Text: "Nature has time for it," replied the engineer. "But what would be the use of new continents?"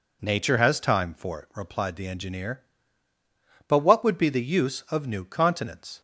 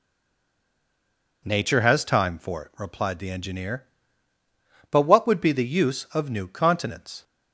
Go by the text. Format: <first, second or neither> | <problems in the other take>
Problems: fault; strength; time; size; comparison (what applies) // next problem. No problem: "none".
first | stays silent before the first word; noticeable; until 1.4 s; 1.4 s long